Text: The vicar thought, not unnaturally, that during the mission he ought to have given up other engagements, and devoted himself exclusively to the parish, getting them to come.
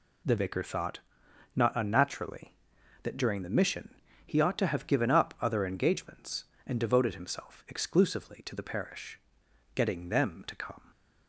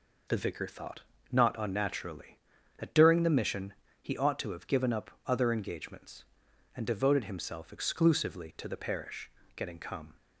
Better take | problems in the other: first | pauses between "mission" and "he"; slight; at 3.7 s; 0.30 s long; slight in the first // pauses between "up" and "other"; slight; at 5.0 s; 0.16 s long // skips "them to"; at 9.7 s

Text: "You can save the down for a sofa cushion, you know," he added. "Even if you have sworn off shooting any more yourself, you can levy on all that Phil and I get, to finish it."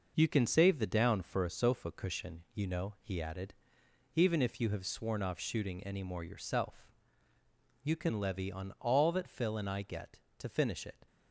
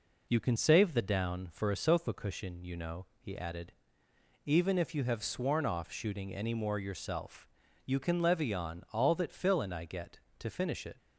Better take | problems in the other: second | gets quieter; noticeable; throughout; 5 dB

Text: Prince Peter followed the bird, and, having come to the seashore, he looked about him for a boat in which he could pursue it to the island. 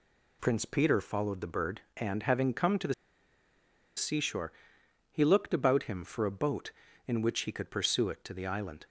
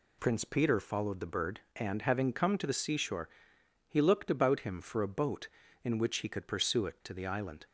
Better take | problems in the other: second | pauses between "the" and "seashore"; at 2.9 s; 1.0 s long

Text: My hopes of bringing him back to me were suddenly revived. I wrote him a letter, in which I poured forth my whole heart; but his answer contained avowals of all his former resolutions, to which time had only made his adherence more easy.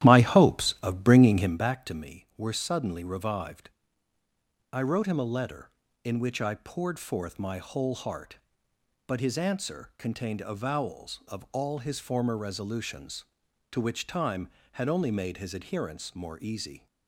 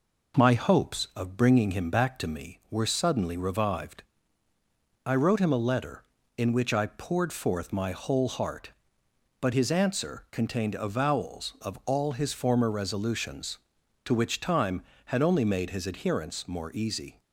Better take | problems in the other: second | starts louder than the rest; strong; until 1.6 s; 12.5 dB

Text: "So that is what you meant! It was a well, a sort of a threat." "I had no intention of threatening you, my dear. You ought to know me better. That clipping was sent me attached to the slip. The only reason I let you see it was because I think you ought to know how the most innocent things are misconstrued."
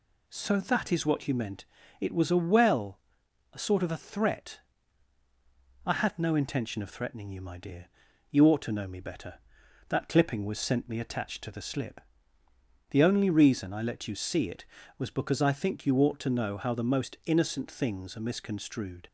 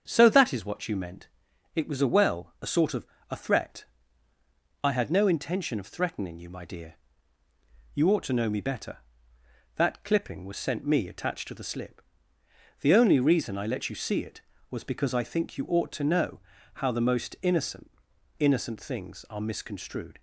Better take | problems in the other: first | starts louder than the rest; strong; until 1.0 s; 7.5 dB // pauses between "of" and "a"; slight; at 3.0 s; 0.24 s long // pauses between "know" and "how"; slight; at 16.3 s; 0.36 s long // says "innocent" twice; at 18.3 s

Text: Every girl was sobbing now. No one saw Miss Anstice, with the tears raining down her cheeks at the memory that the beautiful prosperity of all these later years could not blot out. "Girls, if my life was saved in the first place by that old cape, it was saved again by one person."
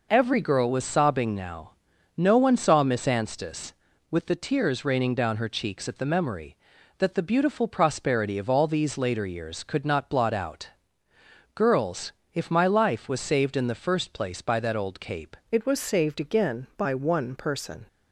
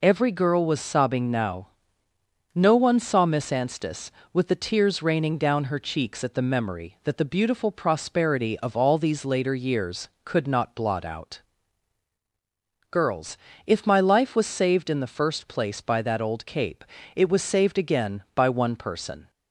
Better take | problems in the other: second | changes voice at "it"; from 15.5 s on; 2.3 s long

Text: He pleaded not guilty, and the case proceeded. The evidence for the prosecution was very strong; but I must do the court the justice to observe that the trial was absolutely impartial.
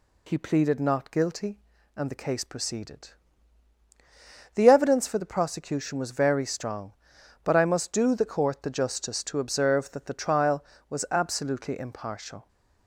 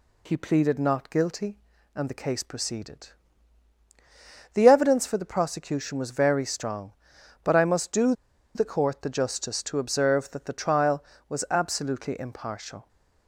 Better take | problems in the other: first | pauses between "do" and "the"; at 8.1 s; 0.42 s long

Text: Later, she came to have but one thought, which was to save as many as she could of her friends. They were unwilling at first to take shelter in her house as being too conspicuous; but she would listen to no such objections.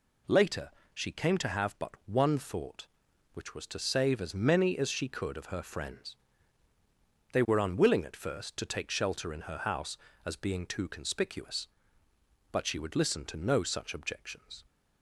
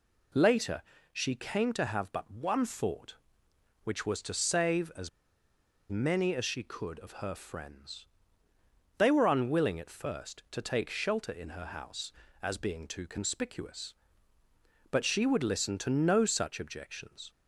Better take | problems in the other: first | pauses between "as" and "many"; noticeable; at 5.0 s; 0.81 s long

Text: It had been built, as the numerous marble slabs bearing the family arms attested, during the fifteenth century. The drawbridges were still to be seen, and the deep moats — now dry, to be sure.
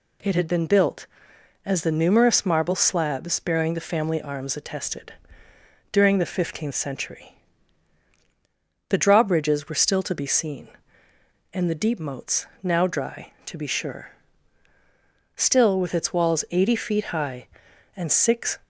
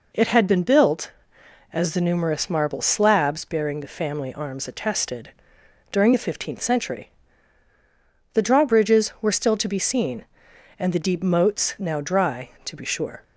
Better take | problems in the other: second | goes on to say "Still with its walls eighty feet high and six"; strong; from 15.3 s on; 3.2 s long

